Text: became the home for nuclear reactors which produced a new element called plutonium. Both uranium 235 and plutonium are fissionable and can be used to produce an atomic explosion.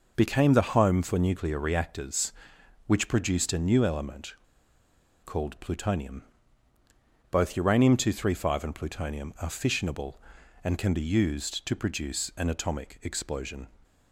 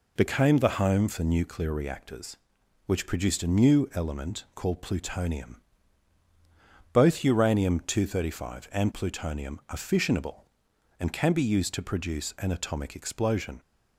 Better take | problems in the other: second | pauses between "element" and "called"; noticeable; at 4.3 s; 0.91 s long

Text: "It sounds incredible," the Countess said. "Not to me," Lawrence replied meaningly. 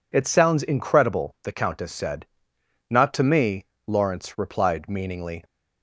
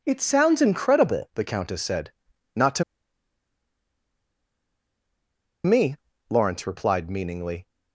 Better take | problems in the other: first | pauses between "to" and "me"; strong; at 2.8 s; 2.8 s long

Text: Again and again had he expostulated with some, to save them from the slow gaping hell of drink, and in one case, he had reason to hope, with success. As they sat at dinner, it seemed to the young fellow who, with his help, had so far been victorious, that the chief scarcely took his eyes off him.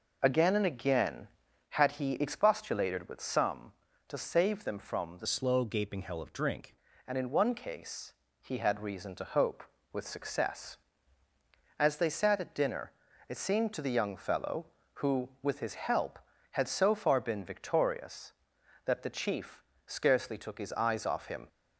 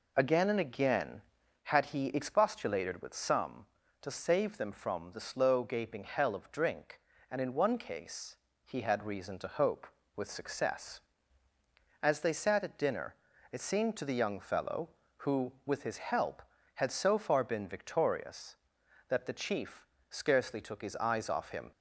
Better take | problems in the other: second | changes voice from "slow" to "drink"; from 5.2 to 6.7 s; 1.5 s long // pauses between "chief" and "scarcely"; slight; at 19.6 s; 0.24 s long; slight in the second

